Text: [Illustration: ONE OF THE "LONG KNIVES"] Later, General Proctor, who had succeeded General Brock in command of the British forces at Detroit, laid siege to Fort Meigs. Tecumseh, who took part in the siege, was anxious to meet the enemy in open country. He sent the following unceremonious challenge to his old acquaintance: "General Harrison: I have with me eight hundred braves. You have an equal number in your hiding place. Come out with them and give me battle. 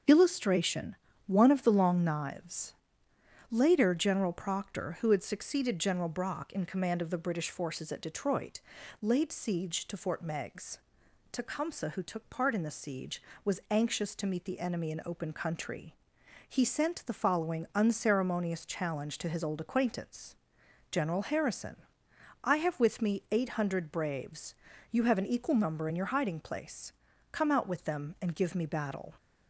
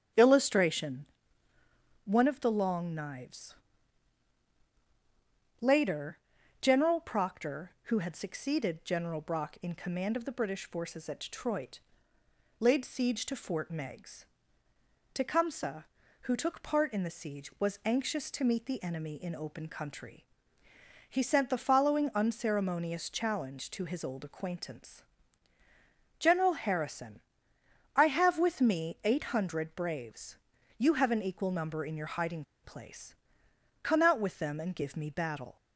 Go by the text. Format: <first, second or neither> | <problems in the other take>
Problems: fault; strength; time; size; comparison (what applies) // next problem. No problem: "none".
first | starts louder than the rest; strong; until 2.1 s; 8 dB; also in the first // pauses between "KNIVES" and "Later"; strong; at 3.5 s; 2.0 s long; noticeable in the first // pauses between "hiding" and "place"; slight; at 32.4 s; 0.20 s long